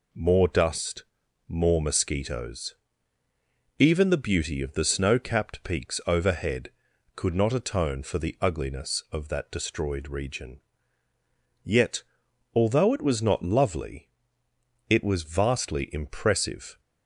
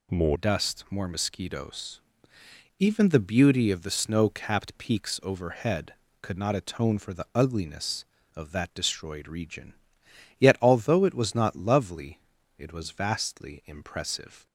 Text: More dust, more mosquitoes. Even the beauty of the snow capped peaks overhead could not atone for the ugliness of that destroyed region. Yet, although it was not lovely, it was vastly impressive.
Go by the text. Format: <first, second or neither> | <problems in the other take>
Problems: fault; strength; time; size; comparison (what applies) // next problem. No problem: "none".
first | changes voice at "dust"; from 0.3 s on; 14.1 s long